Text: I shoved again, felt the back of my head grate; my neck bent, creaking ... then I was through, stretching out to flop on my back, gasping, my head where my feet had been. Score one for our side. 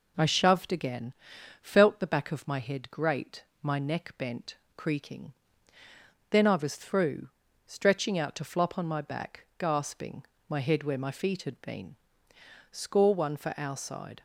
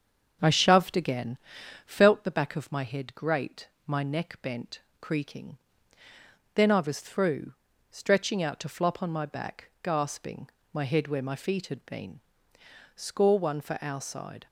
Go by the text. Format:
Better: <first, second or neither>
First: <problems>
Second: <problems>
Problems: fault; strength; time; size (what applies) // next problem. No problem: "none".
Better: first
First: none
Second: starts louder than the rest; until 2.1 s; 7 dB